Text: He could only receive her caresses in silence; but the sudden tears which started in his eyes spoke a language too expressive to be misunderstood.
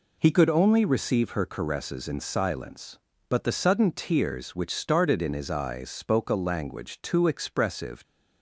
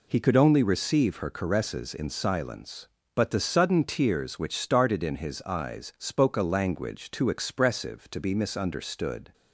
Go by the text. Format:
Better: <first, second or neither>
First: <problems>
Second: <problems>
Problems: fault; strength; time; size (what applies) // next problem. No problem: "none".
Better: second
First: stops before "to be misunderstood"; at 8.0 s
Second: none